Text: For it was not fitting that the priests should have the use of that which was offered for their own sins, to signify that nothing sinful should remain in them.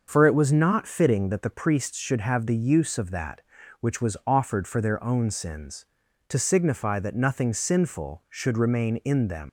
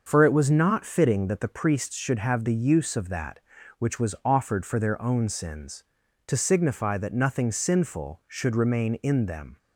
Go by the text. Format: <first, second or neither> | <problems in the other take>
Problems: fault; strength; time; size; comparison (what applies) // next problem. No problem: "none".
second | starts louder than the rest; until 1.0 s; 6.5 dB; also in the second // leaves "them" unfinished; at 9.4 s; 95 ms